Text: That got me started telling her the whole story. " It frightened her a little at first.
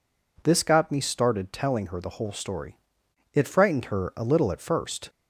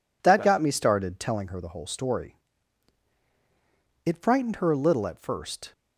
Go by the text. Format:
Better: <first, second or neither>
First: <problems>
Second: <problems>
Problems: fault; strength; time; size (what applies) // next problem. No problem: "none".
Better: second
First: says "This" for "That"; at 0.4 s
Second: none